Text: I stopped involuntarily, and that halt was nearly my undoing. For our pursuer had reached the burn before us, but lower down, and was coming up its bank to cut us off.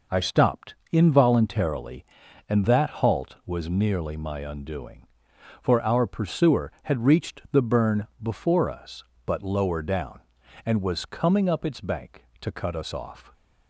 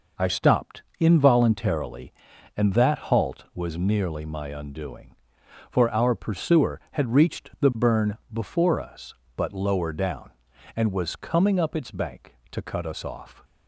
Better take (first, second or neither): neither